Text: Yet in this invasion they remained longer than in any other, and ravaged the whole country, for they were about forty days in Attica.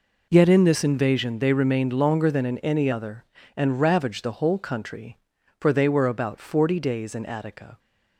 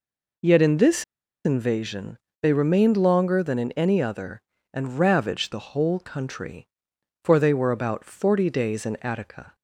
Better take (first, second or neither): first